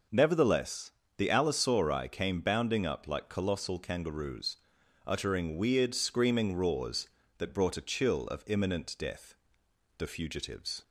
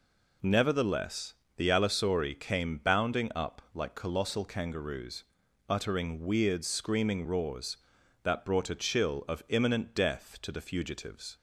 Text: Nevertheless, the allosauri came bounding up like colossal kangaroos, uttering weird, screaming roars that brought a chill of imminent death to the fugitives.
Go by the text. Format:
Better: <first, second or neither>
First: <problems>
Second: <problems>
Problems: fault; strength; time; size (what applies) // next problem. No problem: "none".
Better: second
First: skips "to"; at 9.6 s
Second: none